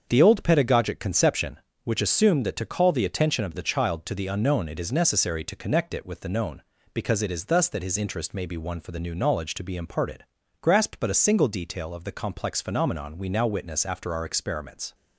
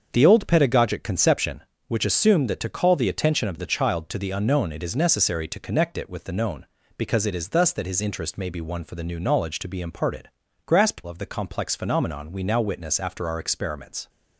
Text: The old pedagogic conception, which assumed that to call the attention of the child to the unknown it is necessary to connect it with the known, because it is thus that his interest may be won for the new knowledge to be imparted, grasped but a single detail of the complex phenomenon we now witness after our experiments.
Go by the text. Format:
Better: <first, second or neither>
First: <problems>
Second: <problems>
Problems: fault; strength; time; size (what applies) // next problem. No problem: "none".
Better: first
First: starts louder than the rest; until 1.1 s; 7 dB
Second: starts louder than the rest; until 1.1 s; 7 dB // skips "but a single detail"; at 11.0 s